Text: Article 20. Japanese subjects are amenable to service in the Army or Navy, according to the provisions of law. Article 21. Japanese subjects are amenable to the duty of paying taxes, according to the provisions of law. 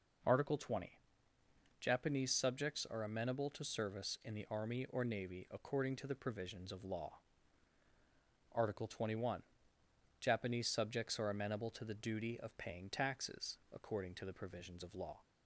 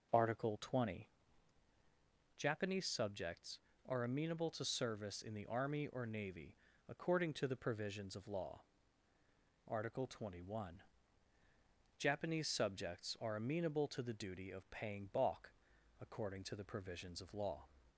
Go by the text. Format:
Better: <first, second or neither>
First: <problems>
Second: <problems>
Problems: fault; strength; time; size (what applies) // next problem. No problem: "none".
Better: first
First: none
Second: says "balk" for "taxes"; at 15.1 s